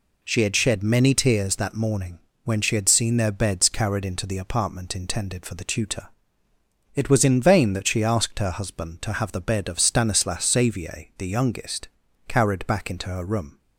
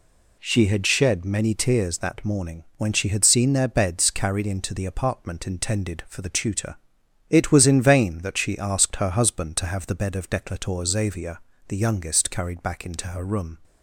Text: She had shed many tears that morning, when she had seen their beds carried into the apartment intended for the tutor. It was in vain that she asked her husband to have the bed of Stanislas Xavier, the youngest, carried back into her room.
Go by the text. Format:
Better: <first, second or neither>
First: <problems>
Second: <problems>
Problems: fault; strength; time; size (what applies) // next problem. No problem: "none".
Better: first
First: none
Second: says "Declator" for "Stanislas"; at 10.2 s